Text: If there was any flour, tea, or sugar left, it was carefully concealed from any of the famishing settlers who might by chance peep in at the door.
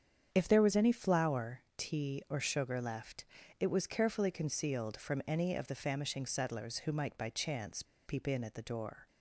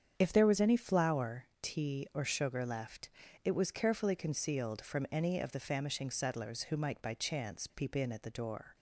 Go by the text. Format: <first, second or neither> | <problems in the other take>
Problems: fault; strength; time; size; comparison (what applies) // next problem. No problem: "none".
second | starts louder than the rest; strong; until 1.3 s; 8 dB; strong in the second // pauses between "chance" and "peep"; slight; at 7.8 s; 0.23 s long